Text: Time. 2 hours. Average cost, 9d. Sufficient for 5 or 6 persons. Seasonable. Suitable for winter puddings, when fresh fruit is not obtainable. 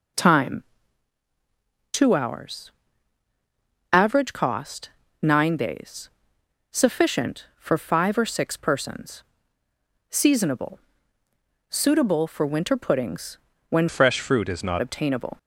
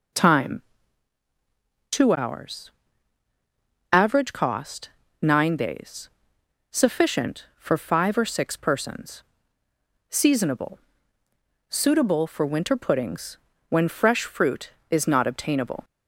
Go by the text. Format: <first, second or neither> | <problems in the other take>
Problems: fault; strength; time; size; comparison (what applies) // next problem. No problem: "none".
second | changes voice from "fresh" to "not"; from 13.8 to 14.8 s; 1.0 s long